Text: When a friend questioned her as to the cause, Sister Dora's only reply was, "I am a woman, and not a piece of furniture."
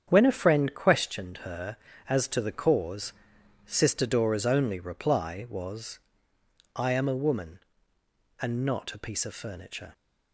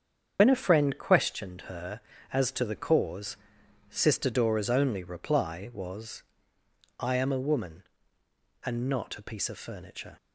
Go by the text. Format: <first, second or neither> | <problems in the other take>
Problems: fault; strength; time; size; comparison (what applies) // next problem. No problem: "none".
first | loses the start of "When"; at 0.3 s; 75 ms // starts louder than the rest; strong; until 1.4 s; 7.5 dB; strong in the first